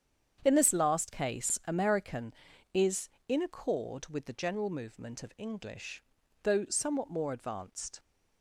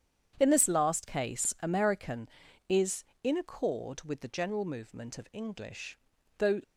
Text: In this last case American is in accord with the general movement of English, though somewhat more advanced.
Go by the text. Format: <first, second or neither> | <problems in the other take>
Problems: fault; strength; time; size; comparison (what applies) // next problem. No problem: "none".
first | starts louder than the rest; strong; until 1.4 s; 8.5 dB; strong in the first // stops before "somewhat more advanced"; at 6.6 s